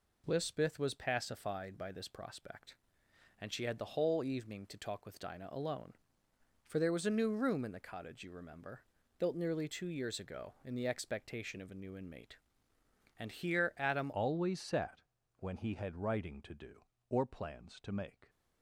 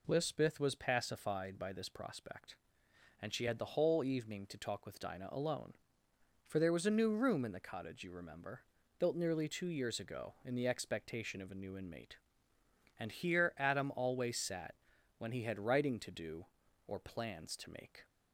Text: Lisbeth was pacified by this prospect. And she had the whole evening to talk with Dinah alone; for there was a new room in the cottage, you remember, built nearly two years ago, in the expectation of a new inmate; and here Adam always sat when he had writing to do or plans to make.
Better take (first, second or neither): second